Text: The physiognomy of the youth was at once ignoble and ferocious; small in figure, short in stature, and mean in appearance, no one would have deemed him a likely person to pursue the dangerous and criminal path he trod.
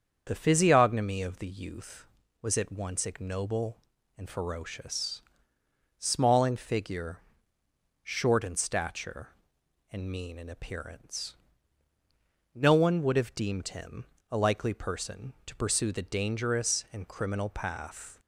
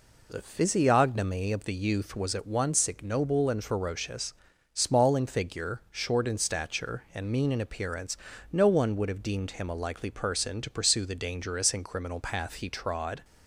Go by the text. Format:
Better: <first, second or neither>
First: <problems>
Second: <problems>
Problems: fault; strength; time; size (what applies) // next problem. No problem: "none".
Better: second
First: starts louder than the rest; strong; until 1.2 s; 7 dB // pauses between "him" and "a"; slight; at 14.0 s; 0.26 s long // stops before "he trod"; at 18.1 s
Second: none